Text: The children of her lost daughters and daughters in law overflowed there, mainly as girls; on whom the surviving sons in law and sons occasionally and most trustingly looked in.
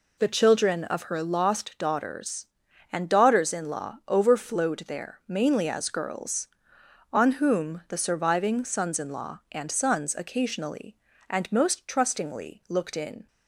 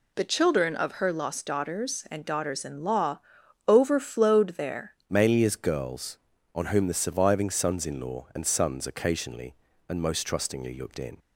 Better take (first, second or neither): first